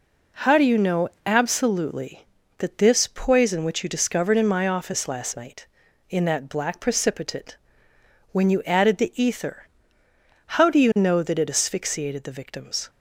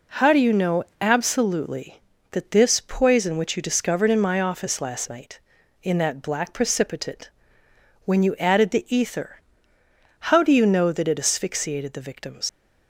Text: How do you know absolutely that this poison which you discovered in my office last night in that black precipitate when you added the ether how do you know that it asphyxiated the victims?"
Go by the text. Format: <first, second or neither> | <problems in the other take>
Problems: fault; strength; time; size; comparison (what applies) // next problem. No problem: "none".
first | pauses between "know" and "absolutely"; slight; at 0.8 s; 0.16 s long; slight in the first // pauses between "precipitate" and "when"; noticeable; at 7.2 s; 0.76 s long; noticeable in the first // pauses between "ether" and "how"; noticeable; at 9.4 s; 0.90 s long; noticeable in the first // leaves "victims" unfinished; at 12.4 s; 100 ms